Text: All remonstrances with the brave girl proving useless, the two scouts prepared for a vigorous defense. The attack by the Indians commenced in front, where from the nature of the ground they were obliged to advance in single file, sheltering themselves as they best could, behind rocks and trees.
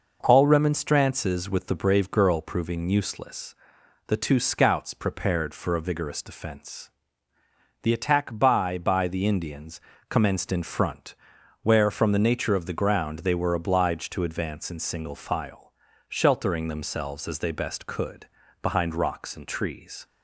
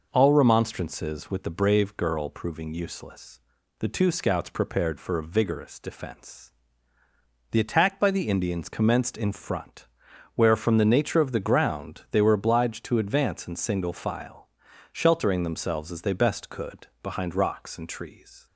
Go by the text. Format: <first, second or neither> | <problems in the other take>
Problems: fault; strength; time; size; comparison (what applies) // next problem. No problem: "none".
second | says "by" twice; at 8.7 s // pauses between "Indians" and "commenced"; slight; at 9.8 s; 0.28 s long